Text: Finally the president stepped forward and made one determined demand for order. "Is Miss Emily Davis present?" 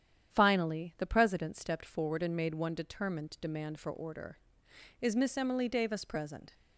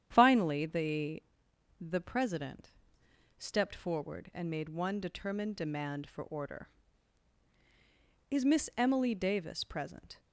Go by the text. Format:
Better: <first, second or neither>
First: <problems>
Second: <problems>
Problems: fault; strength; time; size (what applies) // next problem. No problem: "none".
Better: first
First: starts louder than the rest; strong; until 1.3 s; 9 dB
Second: starts louder than the rest; strong; until 1.1 s; 9.5 dB // says "the" twice; at 1.7 s // pauses between "president" and "stepped"; noticeable; at 2.7 s; 0.66 s long